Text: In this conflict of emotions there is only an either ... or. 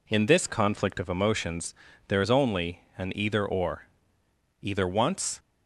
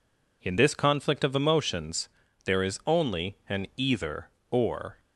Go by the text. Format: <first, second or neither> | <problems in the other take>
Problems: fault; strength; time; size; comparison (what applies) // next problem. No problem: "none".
second | pauses between "emotions" and "there"; slight; at 1.7 s; 0.34 s long; also in the second // pauses between "only" and "an"; slight; at 2.8 s; 0.16 s long // goes on to say "Either once"; noticeable; from 4.6 s on; 0.78 s long